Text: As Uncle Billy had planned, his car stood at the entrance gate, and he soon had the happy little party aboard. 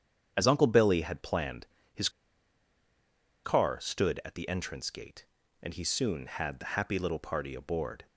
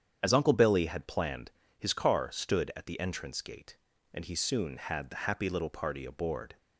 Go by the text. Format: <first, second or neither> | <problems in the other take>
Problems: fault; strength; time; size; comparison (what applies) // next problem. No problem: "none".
second | starts louder than the rest; strong; until 1.3 s; 8 dB; strong in the second // pauses between "his" and "car"; strong; at 2.0 s; 1.3 s long